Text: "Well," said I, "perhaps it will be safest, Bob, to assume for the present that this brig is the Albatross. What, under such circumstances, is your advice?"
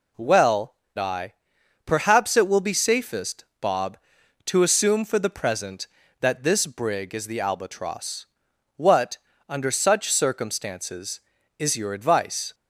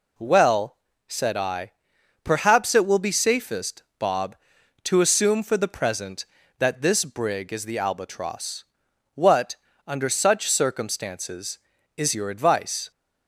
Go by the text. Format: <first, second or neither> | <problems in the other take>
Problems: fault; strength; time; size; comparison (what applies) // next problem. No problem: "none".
second | skips "said"; at 0.8 s